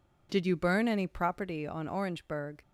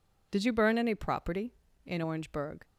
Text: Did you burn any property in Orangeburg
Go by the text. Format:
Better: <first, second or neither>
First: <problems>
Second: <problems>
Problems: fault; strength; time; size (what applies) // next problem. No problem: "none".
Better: second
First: says "on" for "in"; at 1.6 s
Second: none